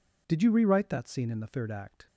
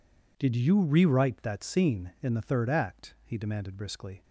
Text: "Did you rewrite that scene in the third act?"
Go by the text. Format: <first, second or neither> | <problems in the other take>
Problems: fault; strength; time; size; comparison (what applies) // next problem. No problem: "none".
first | goes on to say "he demanded briskly"; noticeable; from 3.2 s on; 1.0 s long